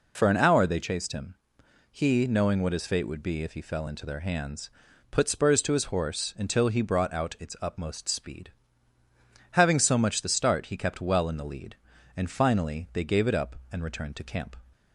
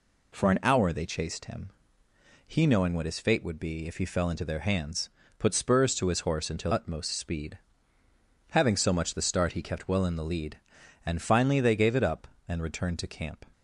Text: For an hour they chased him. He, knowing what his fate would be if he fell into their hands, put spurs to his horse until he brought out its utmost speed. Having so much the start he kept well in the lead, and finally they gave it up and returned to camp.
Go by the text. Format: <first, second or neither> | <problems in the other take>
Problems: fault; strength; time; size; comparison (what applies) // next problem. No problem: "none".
first | skips "he brought out its"; at 6.7 s